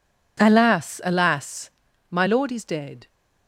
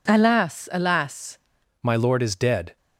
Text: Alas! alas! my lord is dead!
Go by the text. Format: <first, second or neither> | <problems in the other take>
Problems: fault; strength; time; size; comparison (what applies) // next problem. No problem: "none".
first | changes voice at "my"; from 1.8 s on; 0.9 s long